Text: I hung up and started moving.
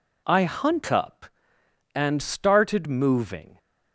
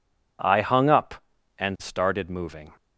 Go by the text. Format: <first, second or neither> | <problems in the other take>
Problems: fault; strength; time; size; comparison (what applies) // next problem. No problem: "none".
second | says "hunt" for "hung"; at 0.4 s